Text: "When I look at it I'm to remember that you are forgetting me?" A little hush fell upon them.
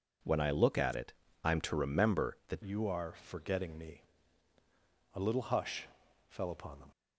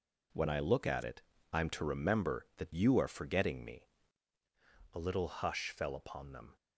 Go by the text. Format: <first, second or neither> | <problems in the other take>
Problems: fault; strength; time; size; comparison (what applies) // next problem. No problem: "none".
second | pauses between "it" and "I'm"; slight; at 1.1 s; 0.28 s long; slight in the second // changes voice at "you"; from 2.6 s on; 4.2 s long // pauses between "hush" and "fell"; at 5.8 s; 0.42 s long